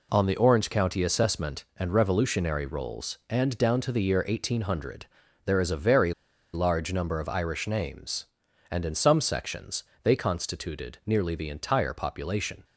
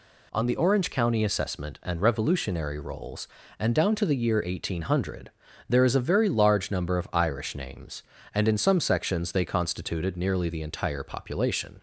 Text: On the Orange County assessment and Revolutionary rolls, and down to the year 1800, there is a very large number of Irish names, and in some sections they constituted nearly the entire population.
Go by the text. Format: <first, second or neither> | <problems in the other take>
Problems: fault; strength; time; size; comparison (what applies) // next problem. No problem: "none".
second | pauses between "very" and "large"; at 6.1 s; 0.41 s long // pauses between "sections" and "they"; slight; at 9.8 s; 0.18 s long